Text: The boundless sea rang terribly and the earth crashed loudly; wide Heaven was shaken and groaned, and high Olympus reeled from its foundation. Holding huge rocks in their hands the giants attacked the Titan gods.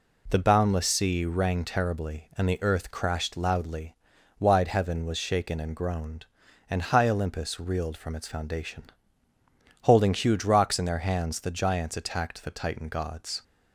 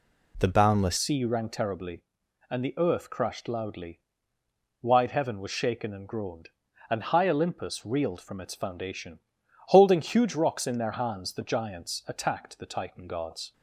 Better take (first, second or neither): first